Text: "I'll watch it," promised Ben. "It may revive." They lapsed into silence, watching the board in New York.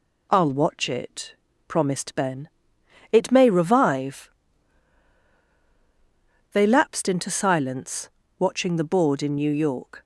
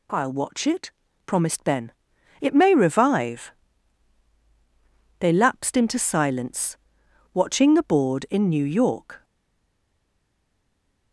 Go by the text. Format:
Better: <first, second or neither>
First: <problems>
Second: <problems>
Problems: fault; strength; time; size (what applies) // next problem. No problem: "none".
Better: first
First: none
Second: stays silent after the last word; noticeable; from 9.2 s on; 1.9 s long